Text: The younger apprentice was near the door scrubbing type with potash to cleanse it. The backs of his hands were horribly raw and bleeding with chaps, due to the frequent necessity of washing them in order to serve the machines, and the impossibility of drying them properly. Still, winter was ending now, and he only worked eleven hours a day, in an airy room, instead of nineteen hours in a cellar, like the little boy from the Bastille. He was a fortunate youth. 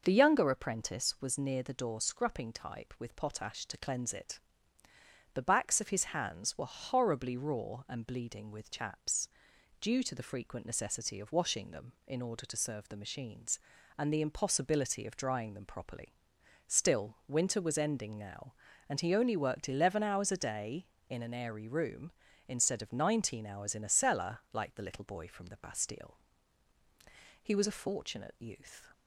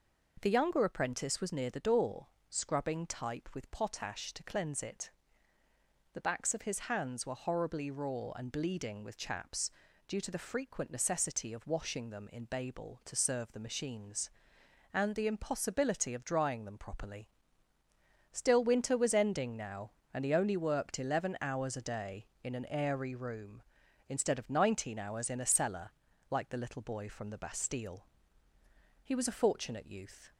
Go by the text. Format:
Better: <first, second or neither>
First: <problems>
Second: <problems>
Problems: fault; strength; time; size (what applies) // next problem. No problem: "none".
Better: first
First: none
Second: pauses between "door" and "scrubbing"; slight; at 2.2 s; 0.22 s long // says "babel" for "order"; at 12.4 s